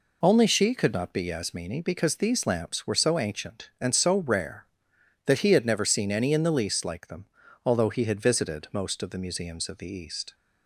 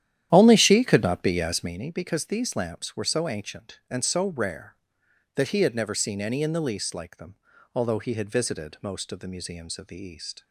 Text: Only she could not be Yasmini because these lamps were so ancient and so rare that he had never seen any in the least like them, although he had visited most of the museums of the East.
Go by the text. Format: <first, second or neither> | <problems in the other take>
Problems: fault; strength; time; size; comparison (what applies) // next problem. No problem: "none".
first | starts louder than the rest; strong; until 1.9 s; 11 dB